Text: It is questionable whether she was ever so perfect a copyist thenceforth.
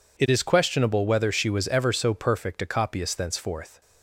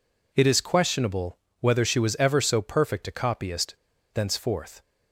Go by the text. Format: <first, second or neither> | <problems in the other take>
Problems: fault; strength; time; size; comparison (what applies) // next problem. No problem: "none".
first | pauses between "questionable" and "whether"; slight; at 1.3 s; 0.22 s long // pauses between "copyist" and "thenceforth"; at 3.7 s; 0.38 s long